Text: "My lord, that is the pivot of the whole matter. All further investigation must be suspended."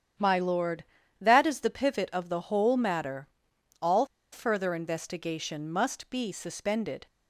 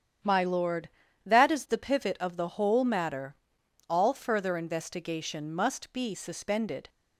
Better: second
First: starts louder than the rest; strong; until 1.5 s; 9 dB // pauses between "All" and "further"; slight; at 4.0 s; 0.25 s long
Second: starts louder than the rest; strong; until 1.6 s; 9 dB

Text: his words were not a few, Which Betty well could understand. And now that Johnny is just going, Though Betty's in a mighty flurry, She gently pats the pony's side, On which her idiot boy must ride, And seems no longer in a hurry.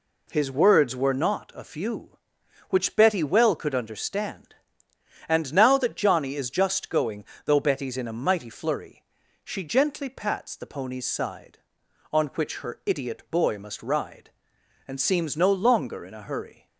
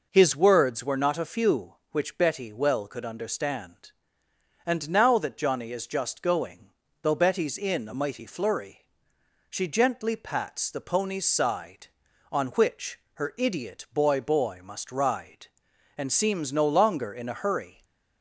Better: first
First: none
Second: pauses between "which" and "her"; slight; at 12.9 s; 0.16 s long // says "boy" twice; at 14.1 s // stays silent after the last word; slight; from 17.7 s on; 0.5 s long

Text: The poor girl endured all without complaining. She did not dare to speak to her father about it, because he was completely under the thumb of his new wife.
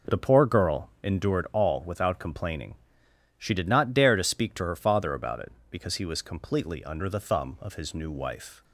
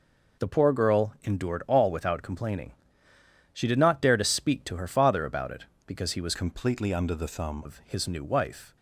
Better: first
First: none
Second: changes voice from "completely" to "thumb"; from 6.3 to 7.6 s; 1.3 s long

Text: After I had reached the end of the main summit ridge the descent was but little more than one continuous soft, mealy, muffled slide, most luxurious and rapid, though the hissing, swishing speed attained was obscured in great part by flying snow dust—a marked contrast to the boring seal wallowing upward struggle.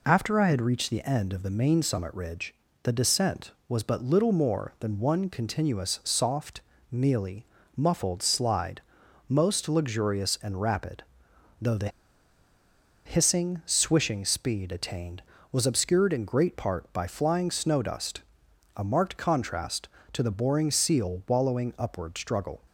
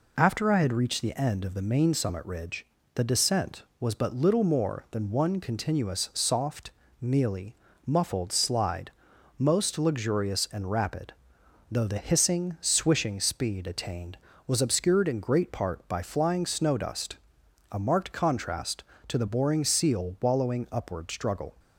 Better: second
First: pauses between "ridge" and "the"; slight; at 2.5 s; 0.28 s long // pauses between "the" and "hissing"; at 11.8 s; 1.1 s long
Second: pauses between "ridge" and "the"; slight; at 2.6 s; 0.28 s long

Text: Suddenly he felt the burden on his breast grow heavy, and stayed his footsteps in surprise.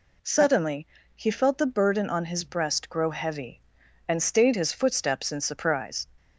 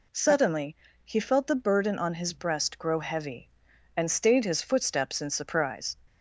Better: neither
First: pauses between "Suddenly" and "he"; slight; at 0.8 s; 0.30 s long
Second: pauses between "Suddenly" and "he"; slight; at 0.7 s; 0.30 s long

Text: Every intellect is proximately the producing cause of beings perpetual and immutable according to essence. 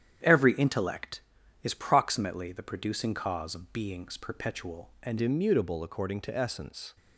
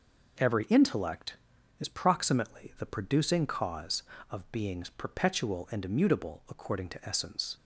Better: second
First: starts louder than the rest; strong; until 1.6 s; 9.5 dB // changes voice at "immutable"; from 5.2 s on; 1.7 s long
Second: none

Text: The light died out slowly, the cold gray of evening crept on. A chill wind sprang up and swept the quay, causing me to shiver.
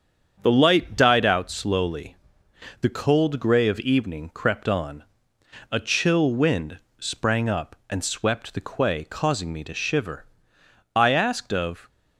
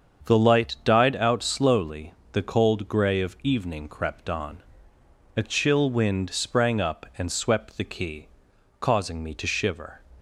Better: second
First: starts louder than the rest; strong; until 1.4 s; 7.5 dB // pauses between "wind" and "sprang"; slight; at 6.7 s; 0.22 s long // goes on to say "I asked of"; noticeable; from 10.9 s on; 0.94 s long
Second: starts louder than the rest; strong; until 1.3 s; 7 dB

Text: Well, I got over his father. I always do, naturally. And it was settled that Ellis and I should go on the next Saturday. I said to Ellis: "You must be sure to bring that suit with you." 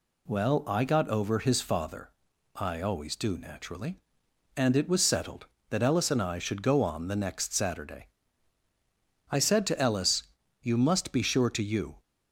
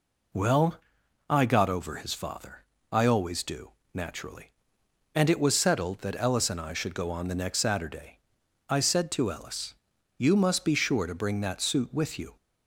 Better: second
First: skips "bring that suit with"; at 11.6 s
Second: none

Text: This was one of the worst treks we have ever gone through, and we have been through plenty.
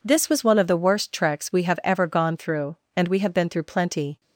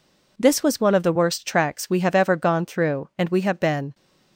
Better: first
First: none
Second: stops before "through plenty"; at 3.9 s

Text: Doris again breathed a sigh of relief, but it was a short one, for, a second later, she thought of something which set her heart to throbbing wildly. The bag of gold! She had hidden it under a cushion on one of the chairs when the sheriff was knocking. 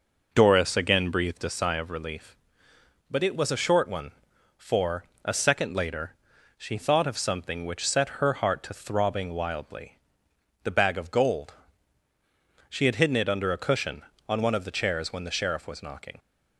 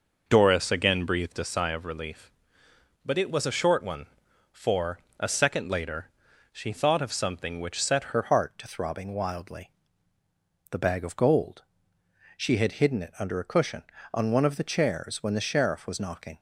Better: first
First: none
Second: changes voice at "her"; from 8.1 s on; 8.2 s long

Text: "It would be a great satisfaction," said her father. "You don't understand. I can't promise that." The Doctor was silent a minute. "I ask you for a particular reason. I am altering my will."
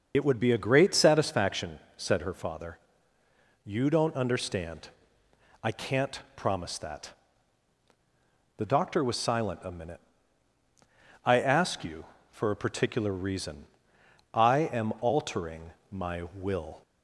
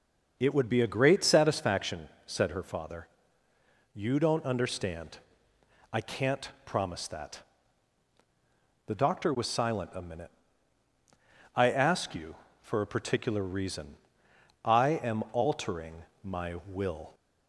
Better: second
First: loses the start of "It"; at 0.1 s; 55 ms // starts louder than the rest; noticeable; until 1.1 s; 6 dB // pauses between "altering" and "my"; slight; at 15.7 s; 0.18 s long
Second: pauses between "altering" and "my"; slight; at 16.0 s; 0.18 s long

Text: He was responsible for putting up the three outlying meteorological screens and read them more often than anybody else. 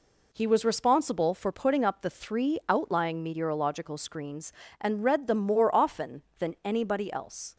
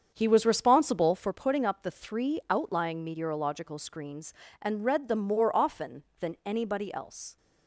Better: first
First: none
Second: starts louder than the rest; strong; until 1.4 s; 7.5 dB

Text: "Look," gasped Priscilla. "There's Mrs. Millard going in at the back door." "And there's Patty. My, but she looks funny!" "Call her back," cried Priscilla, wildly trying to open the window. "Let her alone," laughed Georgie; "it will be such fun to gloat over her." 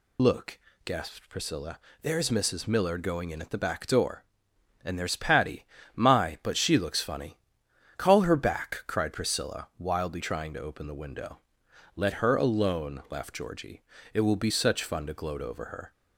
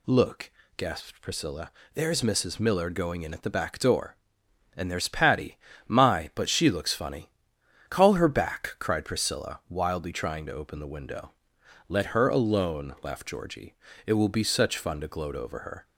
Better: second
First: loses the start of "Look"; at 0.1 s; 55 ms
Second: none

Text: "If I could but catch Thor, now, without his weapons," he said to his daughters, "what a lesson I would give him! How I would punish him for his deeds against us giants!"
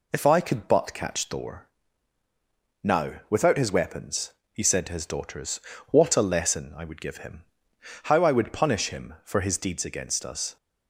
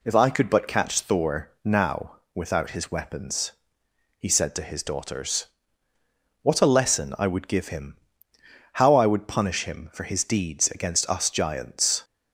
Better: second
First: stops before "giants"; at 10.5 s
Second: none

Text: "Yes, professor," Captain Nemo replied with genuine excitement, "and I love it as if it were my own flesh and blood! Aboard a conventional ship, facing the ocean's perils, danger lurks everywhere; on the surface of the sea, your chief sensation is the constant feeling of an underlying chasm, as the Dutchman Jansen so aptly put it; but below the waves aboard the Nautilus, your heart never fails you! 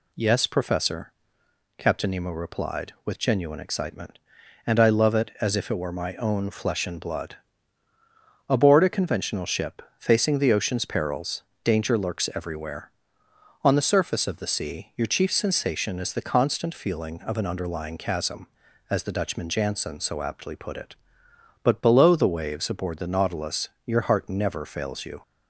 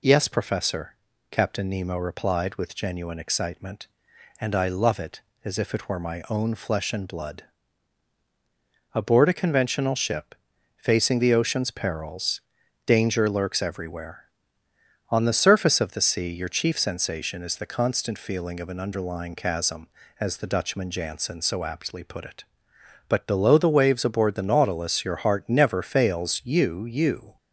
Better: first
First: none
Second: says "you" twice; at 26.8 s

